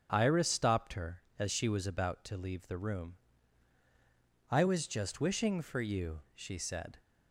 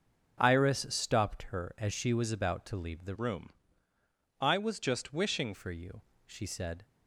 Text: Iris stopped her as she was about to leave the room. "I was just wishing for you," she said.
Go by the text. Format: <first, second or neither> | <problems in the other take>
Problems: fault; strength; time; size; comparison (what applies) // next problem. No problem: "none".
first | starts louder than the rest; until 1.4 s; 6.5 dB; strong in the first // changes voice from "room" to "wishing"; from 3.1 to 5.5 s; 2.4 s long